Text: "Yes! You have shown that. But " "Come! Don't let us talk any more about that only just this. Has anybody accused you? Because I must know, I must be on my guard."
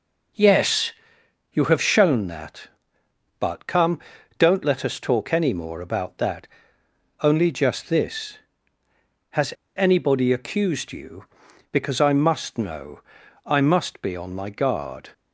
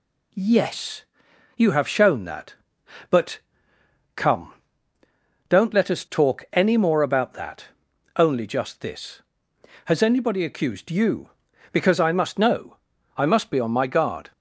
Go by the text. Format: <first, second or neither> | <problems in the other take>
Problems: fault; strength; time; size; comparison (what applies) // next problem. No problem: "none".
second | pauses between "that" and "only"; noticeable; at 6.4 s; 0.72 s long; noticeable in the second // pauses between "Has" and "anybody"; slight; at 9.5 s; 0.24 s long